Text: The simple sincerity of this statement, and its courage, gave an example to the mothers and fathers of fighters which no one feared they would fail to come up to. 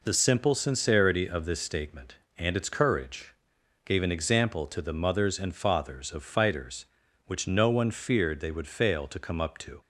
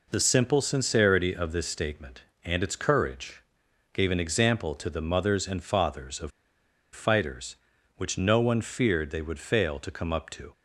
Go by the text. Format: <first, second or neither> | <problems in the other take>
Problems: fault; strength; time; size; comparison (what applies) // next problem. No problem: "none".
first | pauses between "of" and "fighters"; noticeable; at 6.3 s; 0.63 s long